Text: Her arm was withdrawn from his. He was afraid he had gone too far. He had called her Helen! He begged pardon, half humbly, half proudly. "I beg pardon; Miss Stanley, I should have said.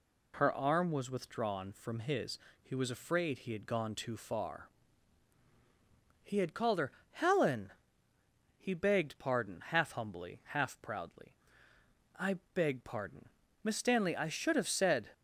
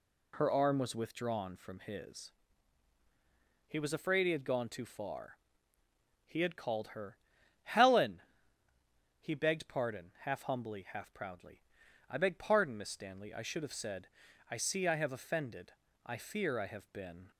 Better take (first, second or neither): first